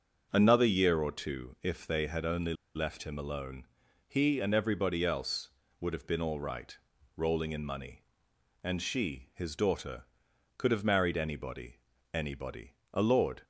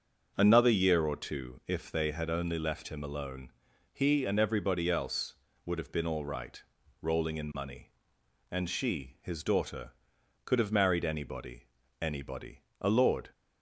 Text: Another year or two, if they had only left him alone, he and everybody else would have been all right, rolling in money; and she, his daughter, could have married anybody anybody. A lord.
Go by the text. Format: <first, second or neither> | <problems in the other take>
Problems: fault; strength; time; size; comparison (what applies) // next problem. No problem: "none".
second | starts louder than the rest; until 1.3 s; 6 dB; also in the second // pauses between "only" and "left"; slight; at 2.5 s; 0.22 s long // pauses between "anybody" and "anybody"; at 11.7 s; 0.40 s long; also in the second